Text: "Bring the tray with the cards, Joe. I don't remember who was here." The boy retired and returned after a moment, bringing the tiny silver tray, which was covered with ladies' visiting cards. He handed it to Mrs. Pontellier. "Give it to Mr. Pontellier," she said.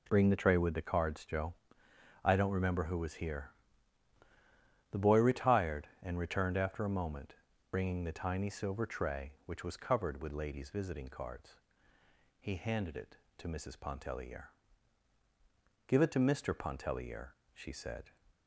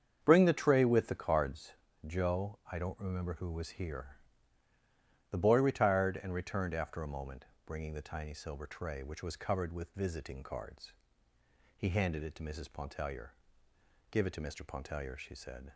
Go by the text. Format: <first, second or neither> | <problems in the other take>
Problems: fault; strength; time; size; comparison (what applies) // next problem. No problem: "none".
first | starts louder than the rest; strong; until 1.2 s; 7.5 dB // skips "ladies"; at 9.9 s